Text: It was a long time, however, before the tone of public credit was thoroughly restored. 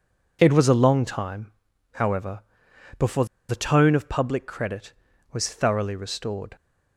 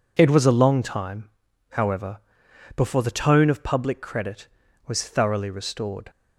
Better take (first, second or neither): second